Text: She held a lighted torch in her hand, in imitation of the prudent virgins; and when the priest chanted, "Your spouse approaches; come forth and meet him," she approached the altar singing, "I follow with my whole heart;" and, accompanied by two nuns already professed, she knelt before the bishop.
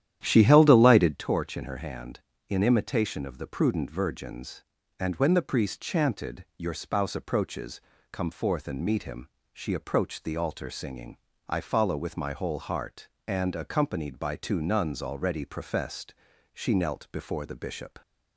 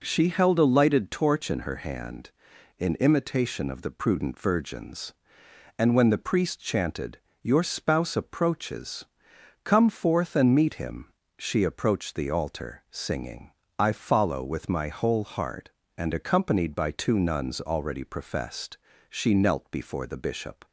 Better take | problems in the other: second | starts louder than the rest; strong; until 1.2 s; 11 dB

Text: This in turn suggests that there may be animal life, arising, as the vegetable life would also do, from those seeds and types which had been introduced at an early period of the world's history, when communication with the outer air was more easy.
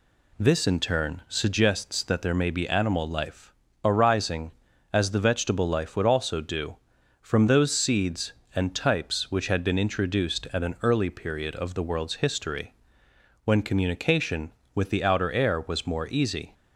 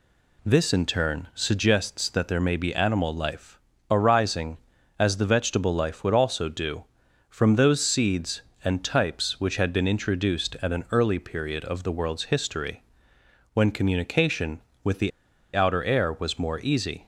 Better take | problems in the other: first | pauses between "the" and "outer"; at 15.1 s; 0.45 s long

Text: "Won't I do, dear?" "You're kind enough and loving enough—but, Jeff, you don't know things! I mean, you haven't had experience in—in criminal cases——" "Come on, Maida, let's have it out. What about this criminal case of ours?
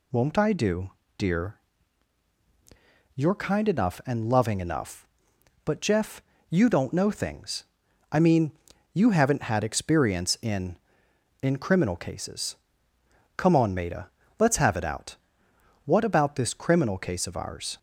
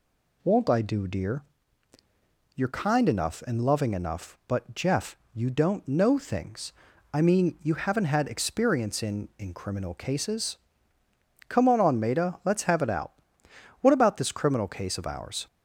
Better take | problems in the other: first | says "on" twice; at 11.7 s

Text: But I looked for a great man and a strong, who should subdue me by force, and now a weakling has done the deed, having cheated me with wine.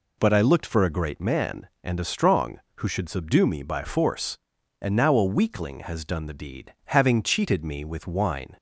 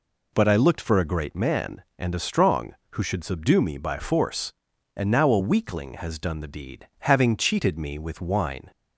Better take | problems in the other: neither | none

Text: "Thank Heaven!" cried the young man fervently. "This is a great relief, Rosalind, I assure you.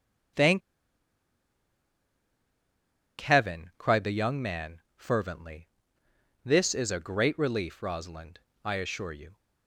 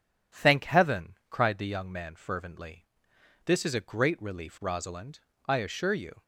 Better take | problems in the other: second | starts louder than the rest; strong; until 4.0 s; 9 dB // pauses between "Thank" and "Heaven"; strong; at 0.6 s; 2.6 s long // pauses between "man" and "fervently"; slight; at 4.8 s; 0.16 s long

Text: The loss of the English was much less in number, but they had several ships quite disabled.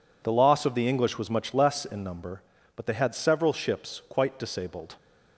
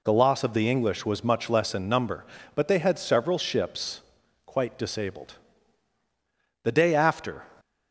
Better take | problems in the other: first | pauses between "ships" and "quite"; noticeable; at 4.0 s; 0.46 s long // goes on to say "The day after"; noticeable; from 6.6 s on; 0.80 s long

